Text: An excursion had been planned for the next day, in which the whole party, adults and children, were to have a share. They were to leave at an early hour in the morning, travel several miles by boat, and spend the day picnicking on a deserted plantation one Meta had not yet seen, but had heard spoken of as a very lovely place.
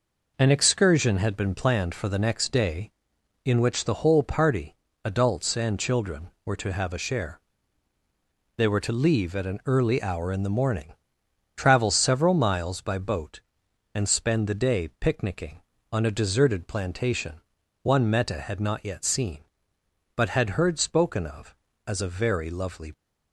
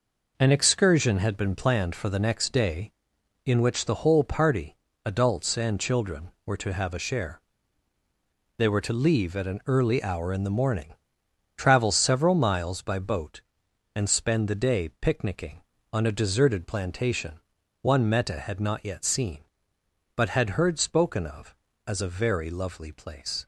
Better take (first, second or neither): second